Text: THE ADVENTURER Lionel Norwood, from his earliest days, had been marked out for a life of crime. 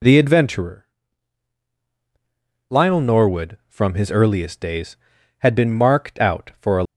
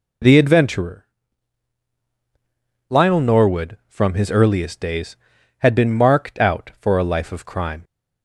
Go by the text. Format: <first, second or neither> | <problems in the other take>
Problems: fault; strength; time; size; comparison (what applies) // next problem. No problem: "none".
second | pauses between "ADVENTURER" and "Lionel"; strong; at 0.8 s; 1.8 s long; strong in the second // stops before "life of crime"; at 6.8 s